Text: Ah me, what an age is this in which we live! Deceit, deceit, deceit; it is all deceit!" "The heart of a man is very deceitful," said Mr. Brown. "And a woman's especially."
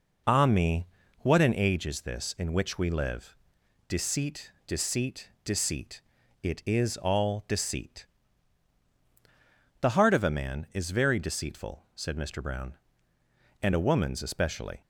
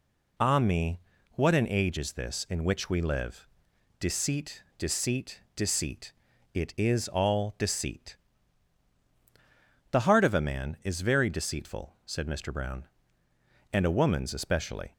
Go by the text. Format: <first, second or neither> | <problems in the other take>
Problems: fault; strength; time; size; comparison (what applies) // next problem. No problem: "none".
second | starts louder than the rest; noticeable; until 1.9 s; 5 dB